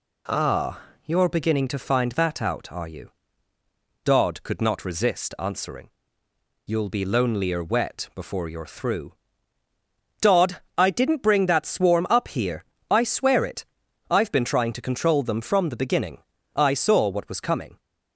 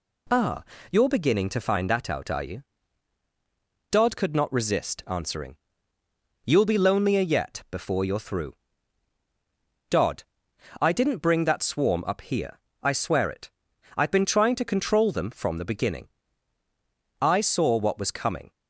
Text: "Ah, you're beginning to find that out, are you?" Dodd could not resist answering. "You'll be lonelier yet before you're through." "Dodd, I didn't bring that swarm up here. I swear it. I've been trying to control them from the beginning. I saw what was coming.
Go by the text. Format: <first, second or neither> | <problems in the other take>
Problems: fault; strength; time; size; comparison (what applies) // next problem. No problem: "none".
second | says "wet" for "yet"; at 7.6 s